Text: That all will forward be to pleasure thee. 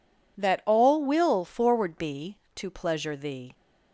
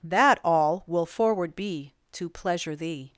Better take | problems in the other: neither | none

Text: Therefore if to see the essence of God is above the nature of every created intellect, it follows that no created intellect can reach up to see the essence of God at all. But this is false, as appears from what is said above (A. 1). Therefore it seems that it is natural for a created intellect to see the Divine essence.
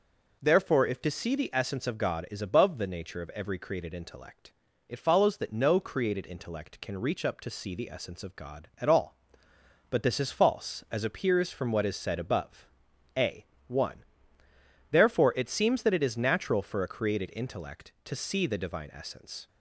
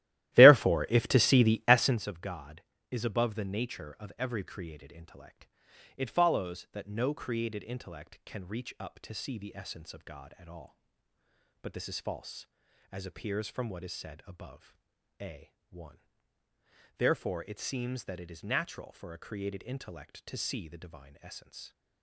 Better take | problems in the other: first | starts louder than the rest; strong; until 2.0 s; 15 dB

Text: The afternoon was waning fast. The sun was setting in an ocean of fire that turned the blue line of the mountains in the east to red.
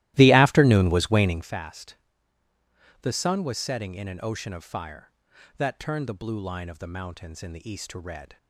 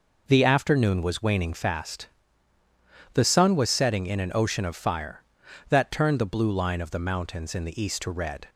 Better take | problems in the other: second | starts louder than the rest; strong; until 1.5 s; 16 dB

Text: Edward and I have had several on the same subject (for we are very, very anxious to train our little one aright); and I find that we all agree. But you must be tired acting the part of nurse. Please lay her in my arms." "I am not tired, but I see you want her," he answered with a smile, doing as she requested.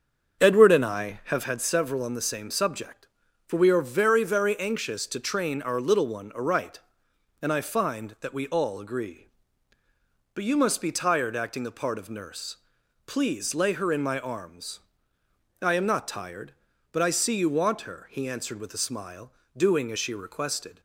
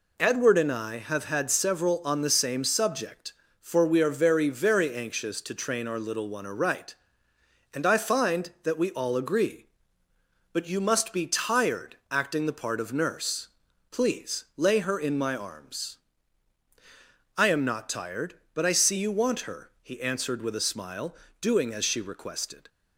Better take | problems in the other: second | starts louder than the rest; until 1.6 s; 7 dB

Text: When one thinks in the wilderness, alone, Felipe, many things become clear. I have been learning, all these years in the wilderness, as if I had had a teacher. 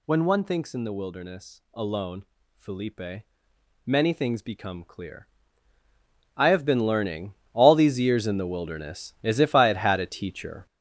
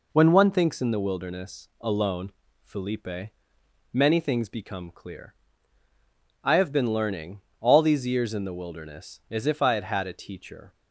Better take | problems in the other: second | gets louder; strong; throughout; 7.5 dB

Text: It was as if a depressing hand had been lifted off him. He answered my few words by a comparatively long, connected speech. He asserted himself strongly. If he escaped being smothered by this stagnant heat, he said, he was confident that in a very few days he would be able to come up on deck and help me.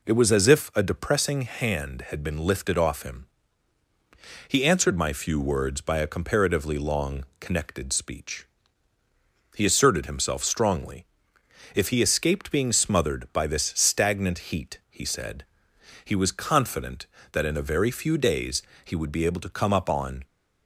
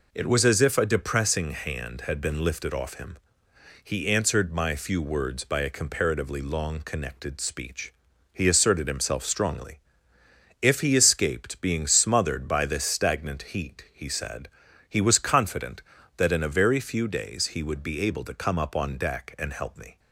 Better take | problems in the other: second | pauses between "days" and "he"; slight; at 18.6 s; 0.20 s long // stops before "deck and help me"; at 20.2 s

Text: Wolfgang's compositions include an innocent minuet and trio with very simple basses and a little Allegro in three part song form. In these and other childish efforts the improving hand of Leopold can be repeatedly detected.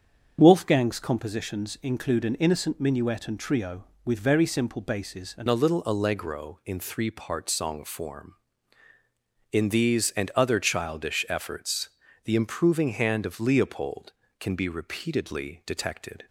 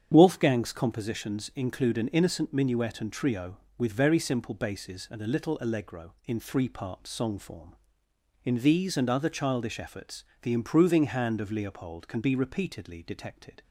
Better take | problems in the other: second | starts louder than the rest; until 1.4 s; 7 dB; strong in the second // changes voice at "a"; from 5.4 s on; 10.8 s long // pauses between "efforts" and "the"; slight; at 11.8 s; 0.36 s long; slight in the second

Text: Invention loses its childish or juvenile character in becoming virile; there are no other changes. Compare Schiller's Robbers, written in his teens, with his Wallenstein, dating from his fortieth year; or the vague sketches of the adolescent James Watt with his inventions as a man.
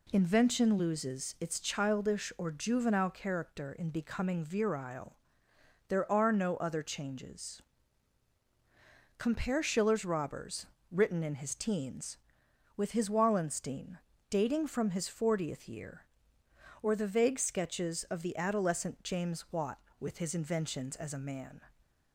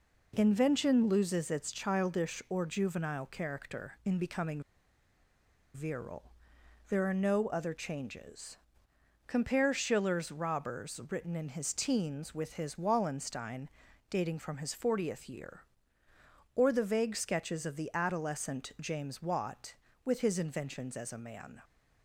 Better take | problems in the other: first | pauses between "becoming" and "virile"; at 4.6 s; 1.1 s long

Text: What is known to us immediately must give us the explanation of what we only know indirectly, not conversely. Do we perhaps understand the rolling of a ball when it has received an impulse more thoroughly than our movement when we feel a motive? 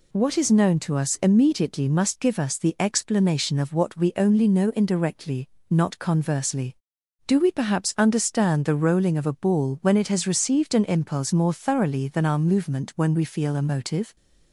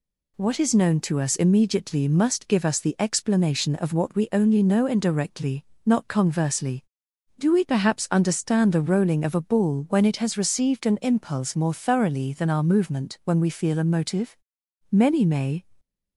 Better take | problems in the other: first | goes on to say "Many may"; noticeable; from 14.9 s on; 0.72 s long

